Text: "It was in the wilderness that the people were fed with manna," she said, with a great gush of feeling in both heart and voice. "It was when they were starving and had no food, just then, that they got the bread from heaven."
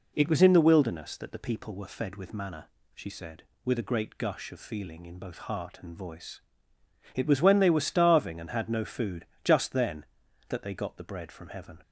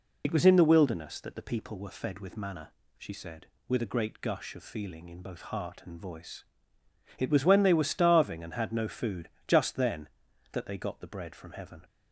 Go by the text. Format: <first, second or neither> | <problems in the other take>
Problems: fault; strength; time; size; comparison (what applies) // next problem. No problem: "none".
first | loses the start of "It"; at 0.2 s; 65 ms